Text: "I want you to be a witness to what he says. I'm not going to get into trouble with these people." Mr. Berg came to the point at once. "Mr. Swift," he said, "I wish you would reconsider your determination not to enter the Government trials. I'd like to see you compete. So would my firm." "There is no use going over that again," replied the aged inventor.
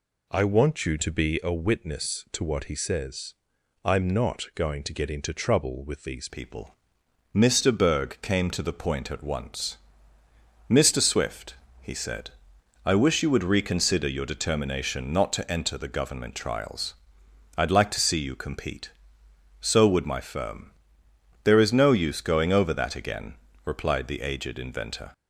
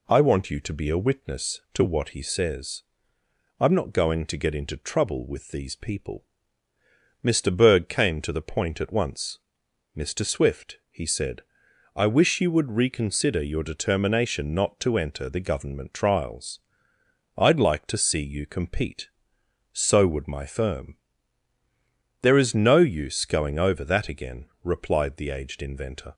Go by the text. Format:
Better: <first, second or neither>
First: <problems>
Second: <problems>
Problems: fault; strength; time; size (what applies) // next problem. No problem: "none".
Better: second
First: changes voice at "people"; from 6.2 s on; 18.9 s long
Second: none